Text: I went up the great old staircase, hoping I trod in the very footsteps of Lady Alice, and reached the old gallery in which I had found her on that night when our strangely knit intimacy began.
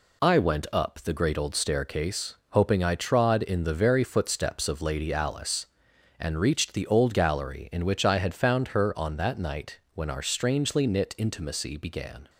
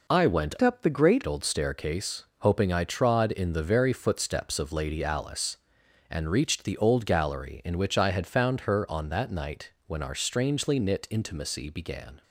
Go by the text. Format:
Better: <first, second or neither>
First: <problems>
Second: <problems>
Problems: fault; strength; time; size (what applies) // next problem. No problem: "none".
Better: first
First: none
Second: changes voice from "up" to "great"; from 0.6 to 1.2 s; 0.6 s long